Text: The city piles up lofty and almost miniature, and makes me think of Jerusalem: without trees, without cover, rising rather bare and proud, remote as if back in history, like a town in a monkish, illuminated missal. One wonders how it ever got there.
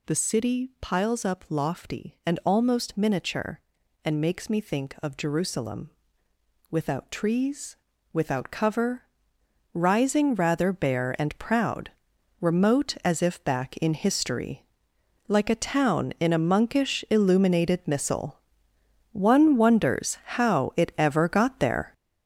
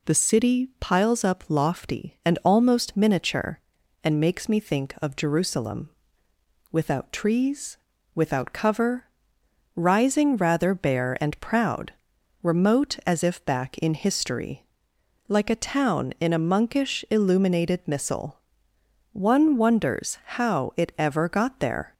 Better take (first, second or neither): second